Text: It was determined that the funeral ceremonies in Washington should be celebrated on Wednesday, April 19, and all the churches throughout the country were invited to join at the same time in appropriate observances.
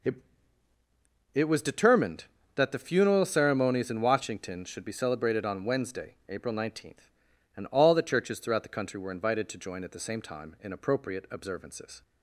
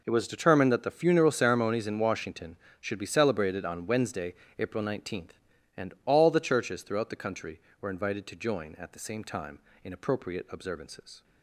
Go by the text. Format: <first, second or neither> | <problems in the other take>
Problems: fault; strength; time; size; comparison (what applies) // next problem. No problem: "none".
second | says "It" twice; at 1.3 s